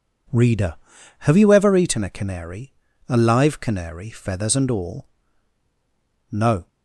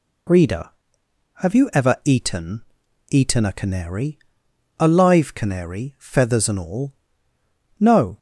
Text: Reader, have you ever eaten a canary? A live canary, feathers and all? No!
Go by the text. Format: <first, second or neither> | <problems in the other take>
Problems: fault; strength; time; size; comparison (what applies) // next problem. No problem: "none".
first | says "eaten" twice; at 3.0 s